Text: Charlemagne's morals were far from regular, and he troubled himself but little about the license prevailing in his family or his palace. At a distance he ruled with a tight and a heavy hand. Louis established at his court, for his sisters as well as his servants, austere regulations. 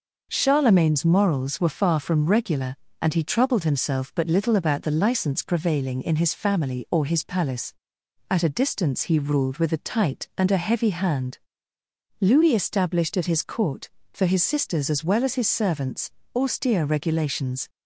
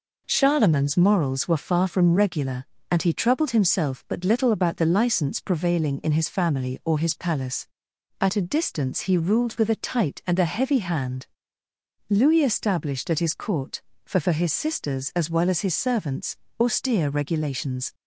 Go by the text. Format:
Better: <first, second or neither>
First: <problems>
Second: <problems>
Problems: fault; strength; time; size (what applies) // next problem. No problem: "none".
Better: first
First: none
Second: says "for" twice; at 14.1 s